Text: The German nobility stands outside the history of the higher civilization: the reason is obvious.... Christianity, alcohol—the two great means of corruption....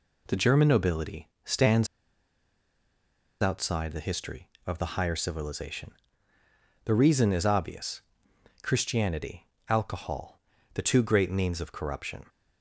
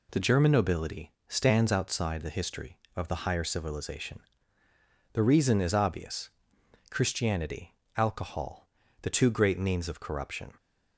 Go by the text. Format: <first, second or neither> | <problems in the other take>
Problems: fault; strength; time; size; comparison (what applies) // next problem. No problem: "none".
second | pauses between "nobility" and "stands"; slight; at 1.2 s; 0.16 s long; slight in the second // pauses between "stands" and "outside"; strong; at 1.8 s; 1.5 s long